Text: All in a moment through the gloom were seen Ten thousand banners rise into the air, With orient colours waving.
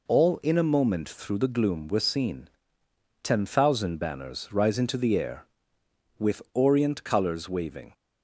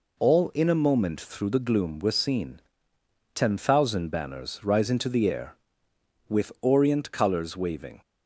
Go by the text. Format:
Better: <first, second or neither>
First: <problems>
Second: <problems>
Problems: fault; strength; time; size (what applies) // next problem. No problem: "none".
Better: neither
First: pauses between "seen" and "Ten"; noticeable; at 2.4 s; 0.76 s long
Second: pauses between "seen" and "Ten"; noticeable; at 2.5 s; 0.76 s long